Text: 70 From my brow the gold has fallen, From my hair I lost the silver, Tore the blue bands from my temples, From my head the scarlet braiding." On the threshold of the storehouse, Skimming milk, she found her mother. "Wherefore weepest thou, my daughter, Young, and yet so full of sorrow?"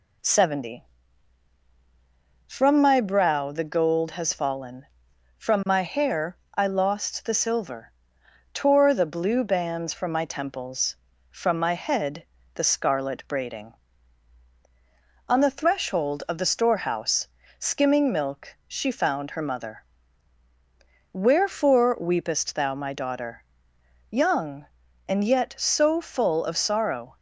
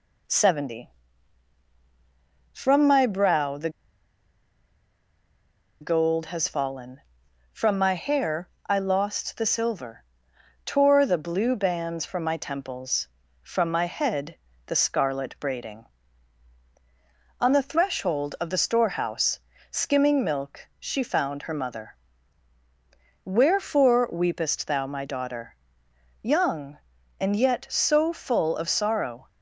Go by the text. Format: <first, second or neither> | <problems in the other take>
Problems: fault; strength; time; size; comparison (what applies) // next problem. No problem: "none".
first | pauses between "the" and "gold"; strong; at 3.6 s; 2.1 s long // pauses between "hair" and "I"; slight; at 8.4 s; 0.18 s long; slight in the first // pauses between "head" and "the"; slight; at 14.3 s; 0.30 s long; slight in the first